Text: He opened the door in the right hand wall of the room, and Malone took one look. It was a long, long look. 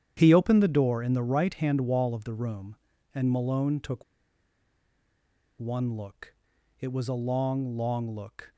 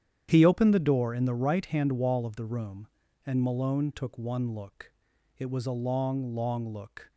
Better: second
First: starts louder than the rest; strong; until 1.1 s; 9.5 dB // pauses between "took" and "one"; strong; at 4.0 s; 1.5 s long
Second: starts louder than the rest; strong; until 1.3 s; 9.5 dB

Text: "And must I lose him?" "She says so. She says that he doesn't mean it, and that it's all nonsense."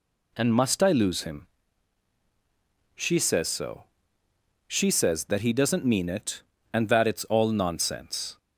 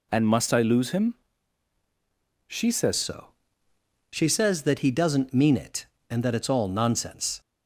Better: first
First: none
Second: changes voice at "so"; from 2.9 s on; 4.4 s long

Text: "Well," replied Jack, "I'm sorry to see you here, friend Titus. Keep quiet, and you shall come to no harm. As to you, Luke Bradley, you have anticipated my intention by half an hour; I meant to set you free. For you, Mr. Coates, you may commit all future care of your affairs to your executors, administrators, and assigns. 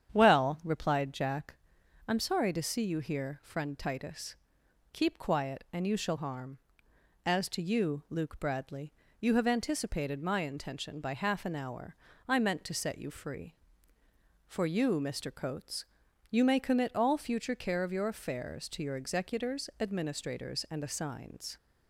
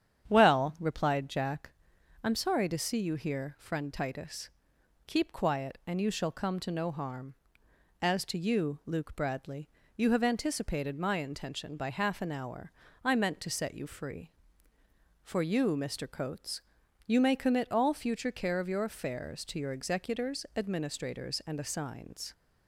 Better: second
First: starts louder than the rest; strong; until 1.1 s; 8.5 dB // skips "come to no"; at 6.1 s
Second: starts louder than the rest; strong; until 1.3 s; 8.5 dB

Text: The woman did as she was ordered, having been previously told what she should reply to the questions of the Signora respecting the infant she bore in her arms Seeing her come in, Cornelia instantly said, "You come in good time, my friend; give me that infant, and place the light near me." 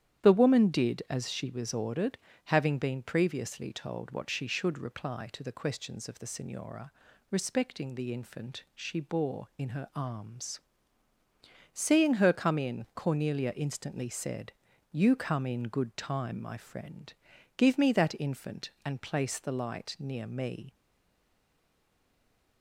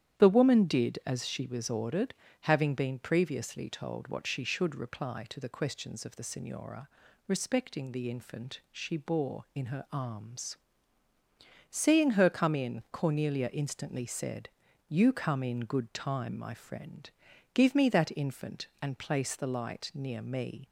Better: second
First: starts louder than the rest; strong; until 1.2 s; 10.5 dB // pauses between "Signora" and "respecting"; at 6.9 s; 0.38 s long // pauses between "arms" and "Seeing"; at 10.5 s; 1.1 s long // stays silent after the last word; noticeable; from 20.7 s on; 1.9 s long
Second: starts louder than the rest; strong; until 1.2 s; 10.5 dB // pauses between "Signora" and "respecting"; at 6.8 s; 0.38 s long // pauses between "arms" and "Seeing"; at 10.5 s; 1.1 s long

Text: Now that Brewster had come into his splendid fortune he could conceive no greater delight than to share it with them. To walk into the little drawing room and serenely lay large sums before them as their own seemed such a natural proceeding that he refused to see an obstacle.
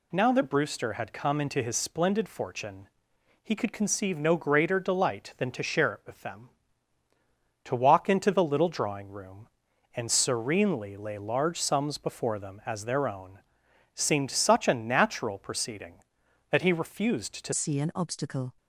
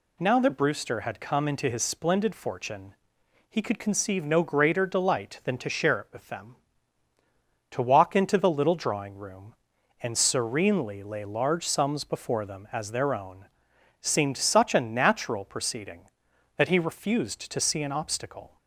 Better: second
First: pauses between "fortune" and "he"; noticeable; at 2.8 s; 0.54 s long // pauses between "own" and "seemed"; noticeable; at 13.3 s; 0.56 s long // changes voice at "see"; from 17.5 s on; 1.0 s long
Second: pauses between "fortune" and "he"; noticeable; at 2.9 s; 0.54 s long // pauses between "own" and "seemed"; noticeable; at 13.4 s; 0.56 s long

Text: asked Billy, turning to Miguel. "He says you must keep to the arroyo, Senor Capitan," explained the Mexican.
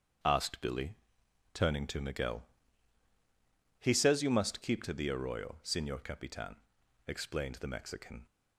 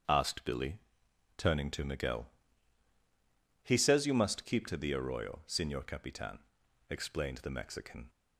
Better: neither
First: starts louder than the rest; strong; until 1.8 s; 8 dB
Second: starts louder than the rest; strong; until 1.6 s; 8 dB

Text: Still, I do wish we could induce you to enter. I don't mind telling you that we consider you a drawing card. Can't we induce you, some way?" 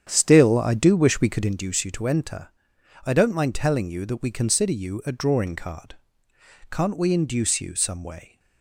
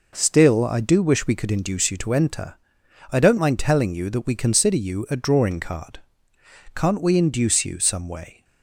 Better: second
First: starts louder than the rest; strong; until 1.5 s; 8.5 dB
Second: none

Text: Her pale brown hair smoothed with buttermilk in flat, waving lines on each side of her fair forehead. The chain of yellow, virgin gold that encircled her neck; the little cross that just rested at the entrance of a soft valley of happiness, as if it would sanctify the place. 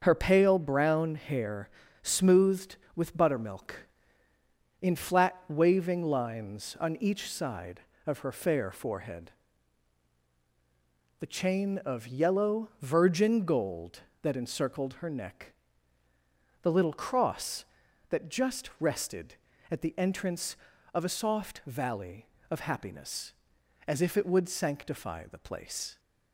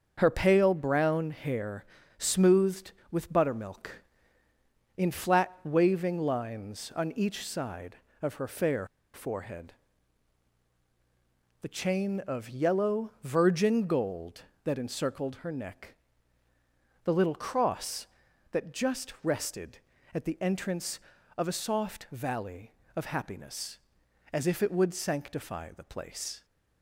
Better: first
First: starts louder than the rest; until 1.0 s; 6.5 dB // pauses between "hair" and "smoothed"; slight; at 1.6 s; 0.34 s long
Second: starts louder than the rest; until 1.1 s; 6.5 dB // pauses between "hair" and "smoothed"; slight; at 1.8 s; 0.34 s long // pauses between "fair" and "forehead"; slight; at 8.8 s; 0.29 s long

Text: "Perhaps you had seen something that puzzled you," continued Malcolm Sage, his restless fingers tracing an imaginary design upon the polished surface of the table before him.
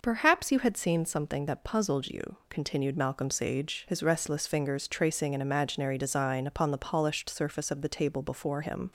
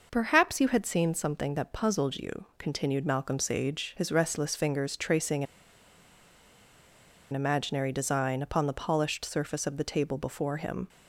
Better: first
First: none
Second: pauses between "tracing" and "an"; strong; at 5.4 s; 1.8 s long

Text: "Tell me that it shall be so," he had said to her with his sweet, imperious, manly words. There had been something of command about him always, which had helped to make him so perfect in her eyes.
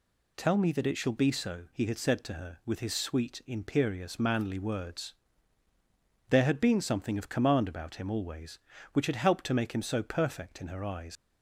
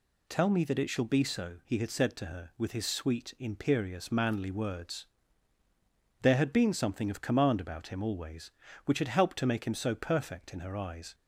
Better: second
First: leaves "eyes" unfinished; at 11.1 s; 70 ms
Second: none

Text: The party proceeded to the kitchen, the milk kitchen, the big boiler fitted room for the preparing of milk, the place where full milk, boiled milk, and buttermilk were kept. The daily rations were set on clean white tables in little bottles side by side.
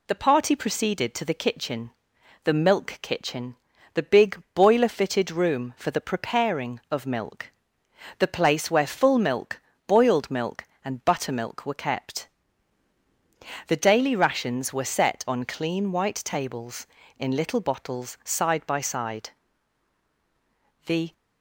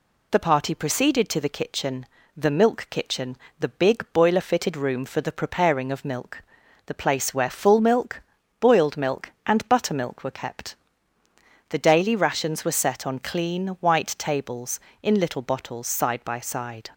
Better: second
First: goes on to say "The"; slight; from 20.8 s on; 0.26 s long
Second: none

